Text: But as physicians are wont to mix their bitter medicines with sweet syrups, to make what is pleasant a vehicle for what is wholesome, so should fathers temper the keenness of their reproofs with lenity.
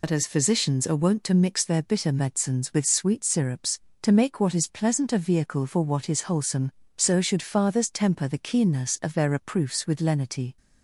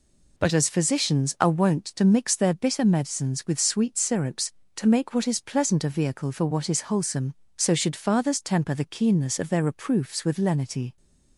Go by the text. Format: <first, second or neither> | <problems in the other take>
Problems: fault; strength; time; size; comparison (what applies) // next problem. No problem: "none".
second | loses the start of "But"; at 0.0 s; 70 ms